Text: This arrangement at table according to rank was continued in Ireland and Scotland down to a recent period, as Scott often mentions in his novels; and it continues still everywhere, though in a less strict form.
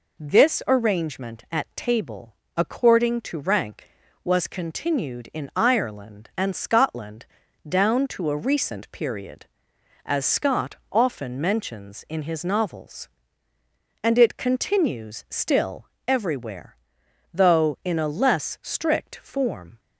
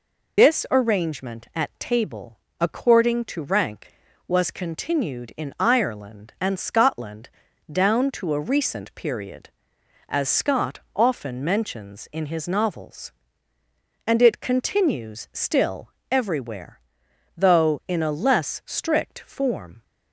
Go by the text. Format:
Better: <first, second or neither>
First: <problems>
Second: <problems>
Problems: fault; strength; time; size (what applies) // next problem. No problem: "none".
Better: first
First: pauses between "table" and "according"; slight; at 2.3 s; 0.20 s long // pauses between "Scotland" and "down"; at 7.2 s; 0.42 s long // pauses between "Scott" and "often"; slight; at 10.7 s; 0.16 s long // pauses between "still" and "everywhere"; slight; at 15.8 s; 0.20 s long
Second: loses the start of "This"; at 0.3 s; 155 ms // pauses between "table" and "according"; slight; at 2.3 s; 0.20 s long // pauses between "Scotland" and "down"; at 7.2 s; 0.42 s long // pauses between "Scott" and "often"; slight; at 10.7 s; 0.16 s long // pauses between "still" and "everywhere"; slight; at 15.9 s; 0.20 s long